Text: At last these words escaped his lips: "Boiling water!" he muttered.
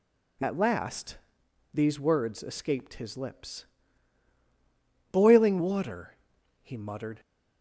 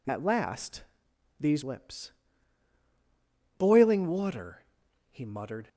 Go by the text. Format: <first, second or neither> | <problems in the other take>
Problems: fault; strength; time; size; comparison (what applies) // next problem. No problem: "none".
first | pauses between "last" and "these"; noticeable; at 0.8 s; 0.56 s long; noticeable in the first // skips "words escaped his"; at 1.6 s